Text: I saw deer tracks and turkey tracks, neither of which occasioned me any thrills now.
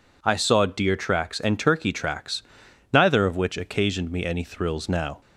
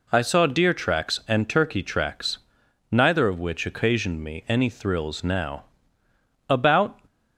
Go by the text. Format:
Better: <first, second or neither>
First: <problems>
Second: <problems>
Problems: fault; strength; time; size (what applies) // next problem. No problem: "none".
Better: first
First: none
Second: goes on to say "About"; from 6.4 s on; 0.50 s long